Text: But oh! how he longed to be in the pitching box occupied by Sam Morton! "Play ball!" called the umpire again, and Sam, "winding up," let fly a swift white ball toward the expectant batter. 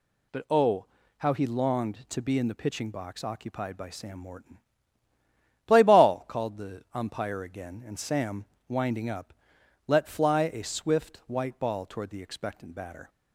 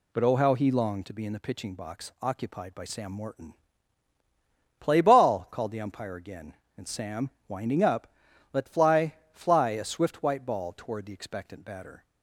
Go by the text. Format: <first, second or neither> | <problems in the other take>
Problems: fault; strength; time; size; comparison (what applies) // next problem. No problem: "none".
first | says "fly" twice; at 9.3 s